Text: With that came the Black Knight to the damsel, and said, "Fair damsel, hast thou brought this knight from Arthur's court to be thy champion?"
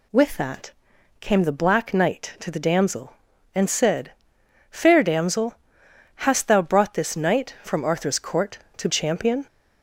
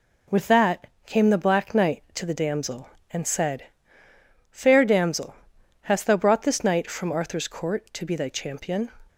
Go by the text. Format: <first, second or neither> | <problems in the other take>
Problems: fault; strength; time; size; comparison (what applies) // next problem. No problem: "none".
second | pauses between "that" and "came"; noticeable; at 0.7 s; 0.50 s long; slight in the second // skips "be thy"; at 8.8 s